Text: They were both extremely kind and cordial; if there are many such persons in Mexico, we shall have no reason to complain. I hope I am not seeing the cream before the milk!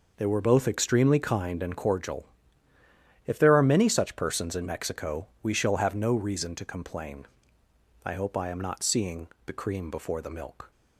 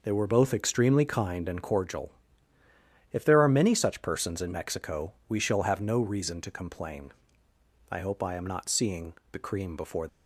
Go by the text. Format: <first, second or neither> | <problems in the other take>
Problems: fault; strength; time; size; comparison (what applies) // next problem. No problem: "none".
first | pauses between "seeing" and "the"; slight; at 9.1 s; 0.18 s long; slight in the first // stops before "the milk"; at 10.0 s